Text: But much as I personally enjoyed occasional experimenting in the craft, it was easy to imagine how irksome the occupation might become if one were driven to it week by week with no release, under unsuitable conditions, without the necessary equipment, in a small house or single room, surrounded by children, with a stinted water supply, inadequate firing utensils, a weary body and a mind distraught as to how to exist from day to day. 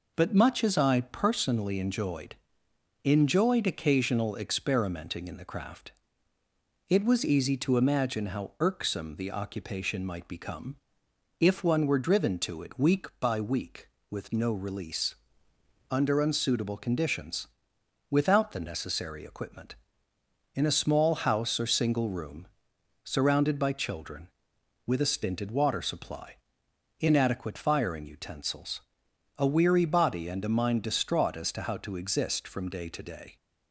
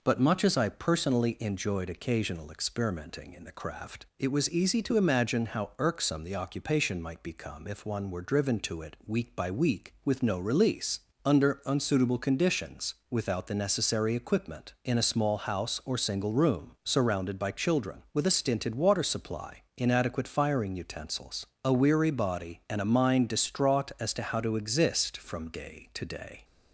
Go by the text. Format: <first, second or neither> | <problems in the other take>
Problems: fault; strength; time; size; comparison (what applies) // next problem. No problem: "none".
second | says "enjoyed" twice; at 3.0 s // pauses between "become" and "if"; noticeable; at 10.7 s; 0.64 s long